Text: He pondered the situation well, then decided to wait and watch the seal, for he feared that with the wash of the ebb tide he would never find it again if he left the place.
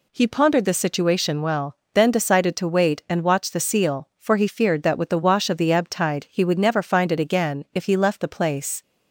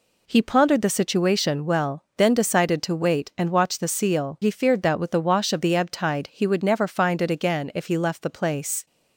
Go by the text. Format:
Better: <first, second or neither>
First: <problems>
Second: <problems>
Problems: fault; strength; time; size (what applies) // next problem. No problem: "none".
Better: first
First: none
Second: skips "for"; at 4.4 s